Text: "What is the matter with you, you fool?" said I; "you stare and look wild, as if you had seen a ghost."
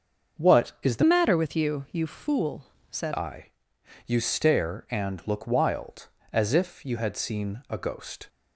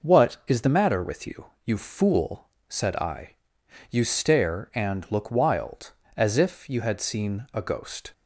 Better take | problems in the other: second | starts louder than the rest; until 1.4 s; 6.5 dB // changes voice from "matter" to "said"; from 1.0 to 3.1 s; 2.1 s long

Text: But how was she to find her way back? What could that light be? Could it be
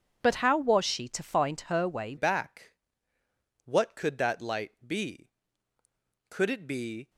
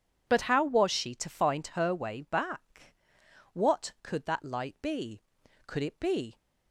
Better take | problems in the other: second | changes voice at "back"; from 2.1 s on; 4.9 s long

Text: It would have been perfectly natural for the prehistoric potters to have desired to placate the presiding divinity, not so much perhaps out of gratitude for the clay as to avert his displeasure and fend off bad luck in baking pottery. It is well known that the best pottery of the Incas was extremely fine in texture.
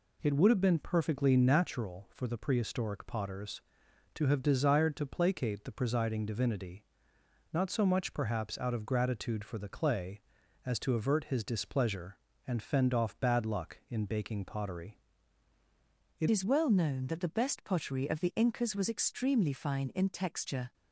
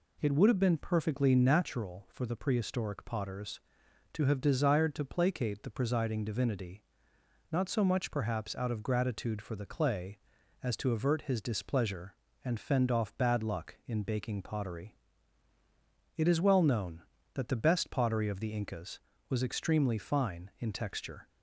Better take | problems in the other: second | changes voice at "is"; from 16.2 s on; 4.5 s long

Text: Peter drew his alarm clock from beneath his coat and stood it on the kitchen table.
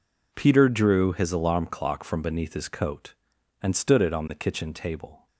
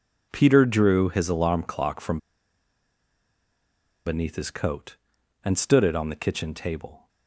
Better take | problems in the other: first | pauses between "from" and "beneath"; strong; at 2.1 s; 1.8 s long

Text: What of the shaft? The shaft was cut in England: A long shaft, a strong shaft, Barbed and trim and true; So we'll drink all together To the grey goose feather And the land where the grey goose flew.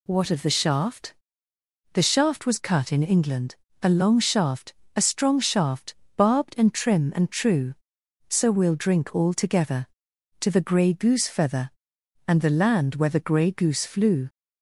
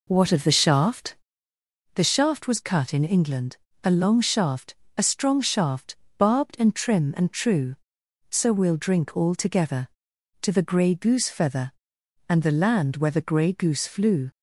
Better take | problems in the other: first | starts louder than the rest; noticeable; until 1.6 s; 4 dB

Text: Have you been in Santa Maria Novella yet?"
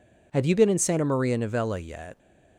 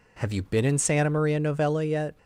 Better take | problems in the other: neither | none

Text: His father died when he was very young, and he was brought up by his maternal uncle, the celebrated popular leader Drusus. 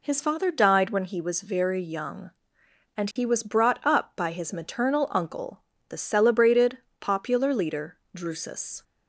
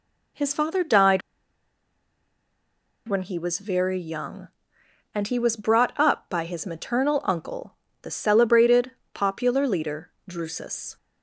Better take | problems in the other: first | pauses between "died" and "when"; strong; at 1.2 s; 1.8 s long // pauses between "celebrated" and "popular"; slight; at 8.9 s; 0.24 s long; slight in the first // pauses between "leader" and "Drusus"; slight; at 10.1 s; 0.18 s long; slight in the first

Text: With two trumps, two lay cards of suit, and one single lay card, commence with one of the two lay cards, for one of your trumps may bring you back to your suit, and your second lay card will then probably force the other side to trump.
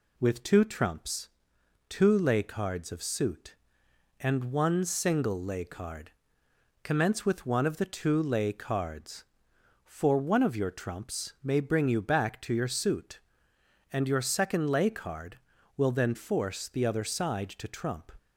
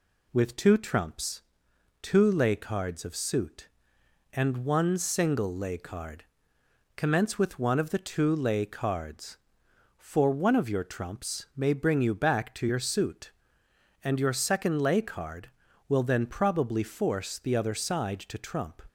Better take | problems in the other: second | skips "probably"; at 16.1 s

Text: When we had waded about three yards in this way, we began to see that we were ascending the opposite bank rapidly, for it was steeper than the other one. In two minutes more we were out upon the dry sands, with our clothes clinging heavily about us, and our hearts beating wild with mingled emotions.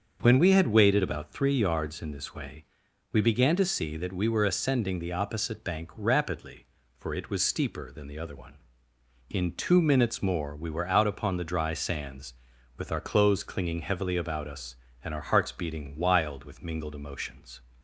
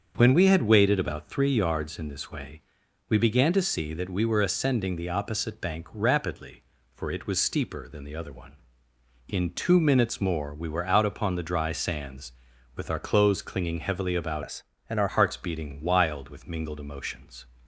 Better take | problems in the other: first | starts louder than the rest; until 1.1 s; 7 dB; also in the first // changes voice from "us" to "our"; from 14.4 to 15.0 s; 0.6 s long

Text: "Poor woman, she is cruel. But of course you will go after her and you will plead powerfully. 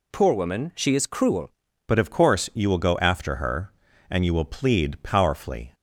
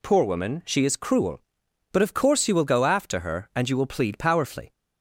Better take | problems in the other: second | changes voice at "But"; from 1.8 s on; 3.9 s long

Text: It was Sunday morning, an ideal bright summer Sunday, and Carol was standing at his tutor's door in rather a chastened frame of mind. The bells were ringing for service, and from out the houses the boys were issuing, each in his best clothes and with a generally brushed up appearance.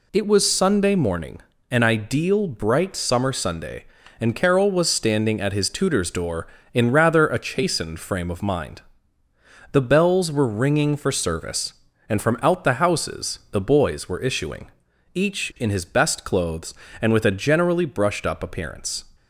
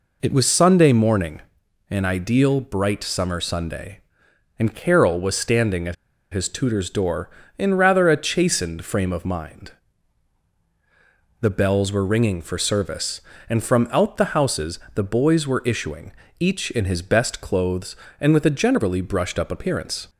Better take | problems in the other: first | pauses between "at" and "his"; at 5.9 s; 0.37 s long // pauses between "houses" and "the"; slight; at 14.7 s; 0.16 s long

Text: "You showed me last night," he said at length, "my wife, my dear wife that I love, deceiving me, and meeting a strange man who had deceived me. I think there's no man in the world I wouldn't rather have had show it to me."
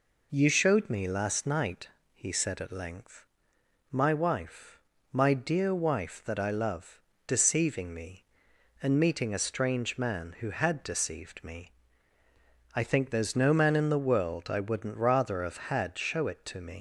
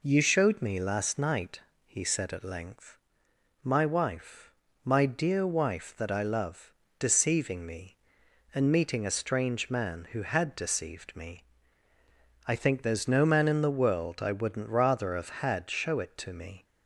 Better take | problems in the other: second | leaves "me" unfinished; at 16.7 s; 115 ms

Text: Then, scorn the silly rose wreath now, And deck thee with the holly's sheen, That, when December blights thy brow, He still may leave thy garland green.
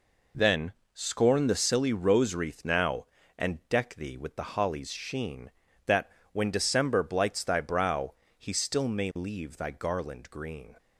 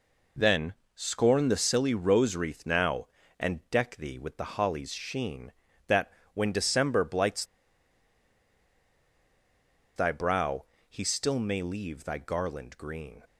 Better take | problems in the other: first | pauses between "blights" and "thy"; strong; at 7.4 s; 2.5 s long

